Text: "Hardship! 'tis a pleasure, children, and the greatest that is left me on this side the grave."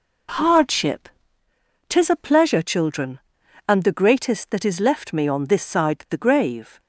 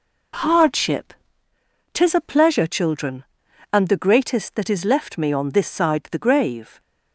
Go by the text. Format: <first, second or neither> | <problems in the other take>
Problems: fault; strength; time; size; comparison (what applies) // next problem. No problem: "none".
neither | none